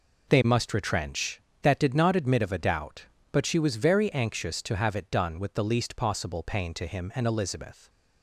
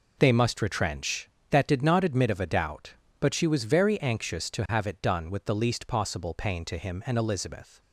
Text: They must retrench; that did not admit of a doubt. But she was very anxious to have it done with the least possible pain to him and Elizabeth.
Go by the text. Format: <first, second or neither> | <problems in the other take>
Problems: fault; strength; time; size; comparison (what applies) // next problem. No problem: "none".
neither | none